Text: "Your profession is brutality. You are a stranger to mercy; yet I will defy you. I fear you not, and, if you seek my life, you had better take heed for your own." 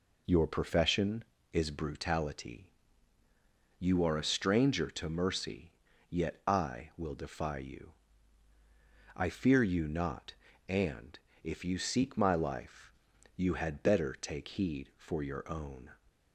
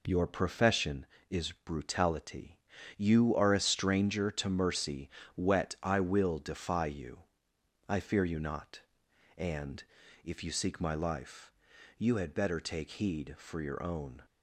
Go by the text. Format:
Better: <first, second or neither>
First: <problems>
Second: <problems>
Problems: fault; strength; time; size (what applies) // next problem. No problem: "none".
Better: first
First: none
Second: says "wet" for "yet"; at 5.3 s